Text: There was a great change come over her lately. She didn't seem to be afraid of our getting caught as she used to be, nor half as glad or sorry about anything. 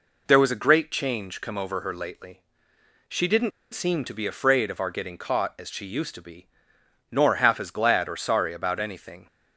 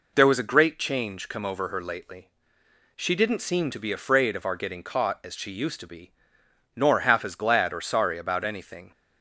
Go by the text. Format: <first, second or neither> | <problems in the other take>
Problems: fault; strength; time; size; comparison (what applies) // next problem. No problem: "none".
second | pauses between "didn't" and "seem"; slight; at 3.5 s; 0.23 s long